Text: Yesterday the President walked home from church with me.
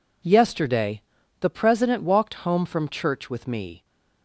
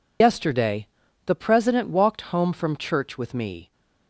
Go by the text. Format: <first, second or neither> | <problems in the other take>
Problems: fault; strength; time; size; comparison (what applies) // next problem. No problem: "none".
first | loses the start of "Yesterday"; at 0.2 s; 105 ms // pauses between "Yesterday" and "the"; at 0.8 s; 0.40 s long; also in the first